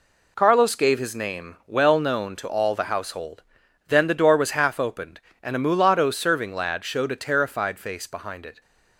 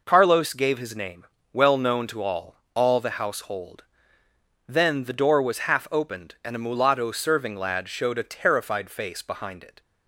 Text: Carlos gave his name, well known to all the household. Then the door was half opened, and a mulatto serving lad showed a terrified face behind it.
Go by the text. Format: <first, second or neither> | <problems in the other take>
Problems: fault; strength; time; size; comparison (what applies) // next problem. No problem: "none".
first | says "all" twice; at 2.7 s